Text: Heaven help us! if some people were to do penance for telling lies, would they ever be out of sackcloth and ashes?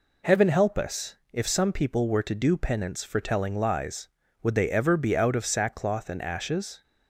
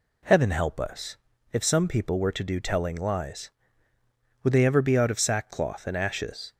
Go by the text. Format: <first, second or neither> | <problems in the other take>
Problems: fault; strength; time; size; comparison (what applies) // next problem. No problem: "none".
first | skips "penance for"; at 2.5 s